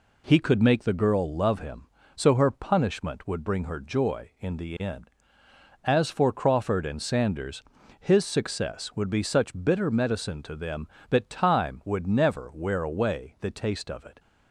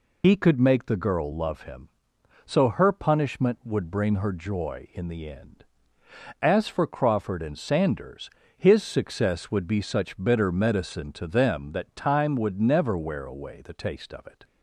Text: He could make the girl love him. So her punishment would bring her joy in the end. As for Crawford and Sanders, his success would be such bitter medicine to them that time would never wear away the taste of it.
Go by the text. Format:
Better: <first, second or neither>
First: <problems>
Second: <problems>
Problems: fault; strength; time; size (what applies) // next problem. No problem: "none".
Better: first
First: none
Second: loses the start of "He"; at 0.2 s; 75 ms